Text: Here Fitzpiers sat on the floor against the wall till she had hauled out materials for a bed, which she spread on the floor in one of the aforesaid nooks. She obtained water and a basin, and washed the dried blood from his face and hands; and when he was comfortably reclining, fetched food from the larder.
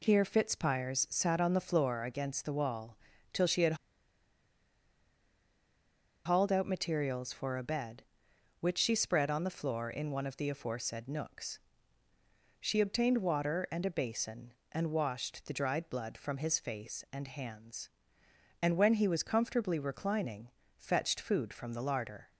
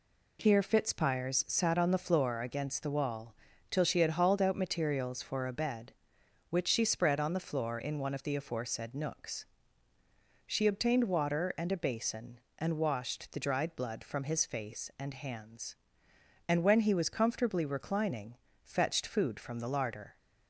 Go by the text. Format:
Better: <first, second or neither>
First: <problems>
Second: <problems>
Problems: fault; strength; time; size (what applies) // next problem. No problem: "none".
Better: second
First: pauses between "wall" and "till"; slight; at 2.9 s; 0.36 s long // pauses between "had" and "hauled"; strong; at 3.7 s; 2.5 s long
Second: pauses between "wall" and "till"; slight; at 3.3 s; 0.36 s long